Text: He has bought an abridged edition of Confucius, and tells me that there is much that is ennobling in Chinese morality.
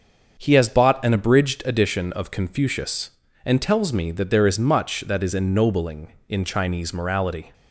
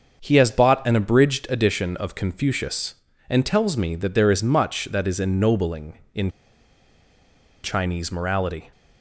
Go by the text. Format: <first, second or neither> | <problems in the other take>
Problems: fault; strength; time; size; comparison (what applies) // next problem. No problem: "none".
first | starts louder than the rest; until 1.2 s; 6.5 dB; also in the first // pauses between "in" and "Chinese"; strong; at 6.2 s; 1.3 s long